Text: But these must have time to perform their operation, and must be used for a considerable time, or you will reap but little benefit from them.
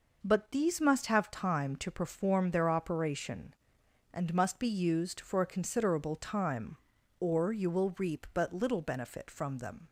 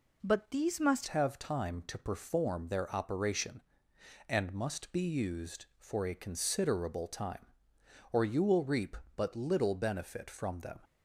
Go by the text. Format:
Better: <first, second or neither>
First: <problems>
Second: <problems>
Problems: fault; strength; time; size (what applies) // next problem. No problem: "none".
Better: first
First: none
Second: changes voice at "have"; from 1.0 s on; 9.7 s long